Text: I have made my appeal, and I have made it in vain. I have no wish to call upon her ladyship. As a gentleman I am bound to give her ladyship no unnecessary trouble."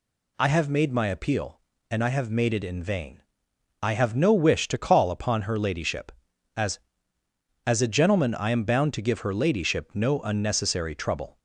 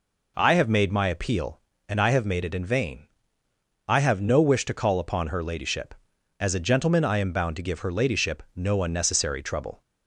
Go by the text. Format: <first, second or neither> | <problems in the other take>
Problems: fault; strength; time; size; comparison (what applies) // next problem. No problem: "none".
second | says "As" twice; at 7.6 s